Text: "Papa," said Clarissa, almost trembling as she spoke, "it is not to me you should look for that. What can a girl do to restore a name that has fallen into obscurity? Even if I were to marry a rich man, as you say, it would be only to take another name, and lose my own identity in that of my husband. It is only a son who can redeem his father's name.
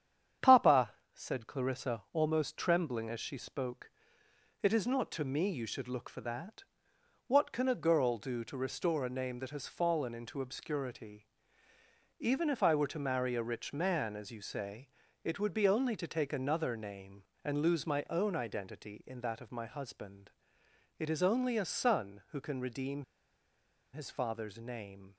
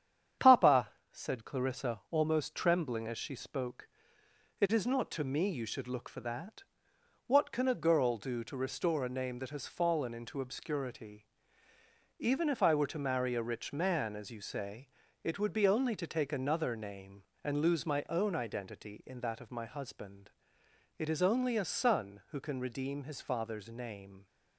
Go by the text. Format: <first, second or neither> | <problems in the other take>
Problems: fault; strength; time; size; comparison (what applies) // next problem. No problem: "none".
second | starts louder than the rest; strong; until 1.6 s; 8.5 dB; strong in the second // pauses between "redeem" and "his"; noticeable; at 23.0 s; 0.89 s long